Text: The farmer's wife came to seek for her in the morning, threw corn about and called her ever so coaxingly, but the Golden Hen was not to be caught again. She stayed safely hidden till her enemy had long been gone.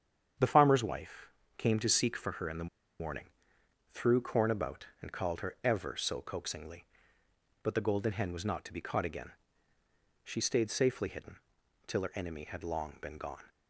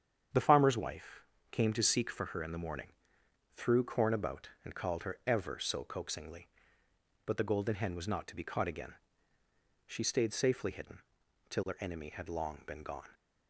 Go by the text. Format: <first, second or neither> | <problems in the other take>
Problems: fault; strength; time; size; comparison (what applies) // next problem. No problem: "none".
second | starts louder than the rest; strong; until 1.6 s; 8 dB; strong in the second // pauses between "wife" and "came"; slight; at 1.3 s; 0.26 s long; slight in the second // pauses between "the" and "morning"; slight; at 2.6 s; 0.33 s long // pauses between "hidden" and "till"; noticeable; at 11.3 s; 0.50 s long; noticeable in the second